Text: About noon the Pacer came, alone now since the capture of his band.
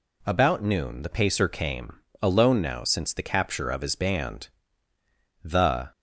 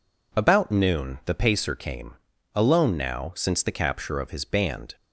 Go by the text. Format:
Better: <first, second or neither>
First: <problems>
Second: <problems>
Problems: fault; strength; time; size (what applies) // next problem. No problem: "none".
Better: second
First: goes on to say "The"; slight; from 5.4 s on; 0.48 s long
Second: none